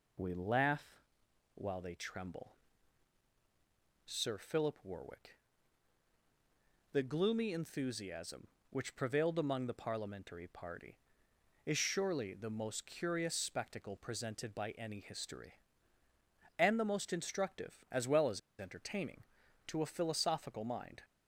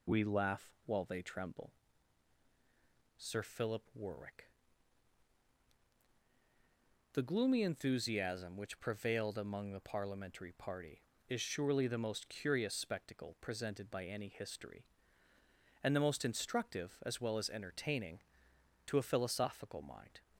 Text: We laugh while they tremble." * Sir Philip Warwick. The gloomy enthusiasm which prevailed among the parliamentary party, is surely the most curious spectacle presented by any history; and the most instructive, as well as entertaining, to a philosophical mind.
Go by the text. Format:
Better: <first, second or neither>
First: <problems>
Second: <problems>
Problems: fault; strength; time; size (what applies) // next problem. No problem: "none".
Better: second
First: pauses between "laugh" and "while"; noticeable; at 0.9 s; 0.56 s long // pauses between "as" and "entertaining"; slight; at 18.3 s; 0.19 s long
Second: pauses between "laugh" and "while"; slight; at 0.7 s; 0.16 s long